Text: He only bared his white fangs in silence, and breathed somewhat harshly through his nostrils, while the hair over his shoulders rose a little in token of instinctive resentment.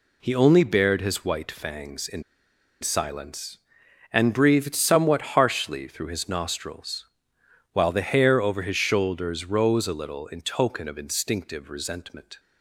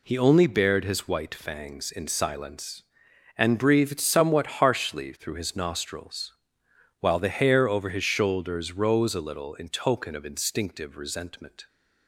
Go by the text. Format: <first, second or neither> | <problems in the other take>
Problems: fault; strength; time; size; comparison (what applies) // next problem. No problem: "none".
second | pauses between "in" and "silence"; noticeable; at 2.2 s; 0.60 s long